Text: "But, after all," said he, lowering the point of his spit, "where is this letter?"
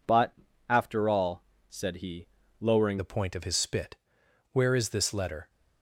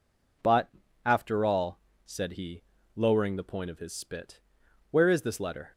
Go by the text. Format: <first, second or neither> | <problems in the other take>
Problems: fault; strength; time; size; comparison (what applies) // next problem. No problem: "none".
second | changes voice at "the"; from 2.9 s on; 2.5 s long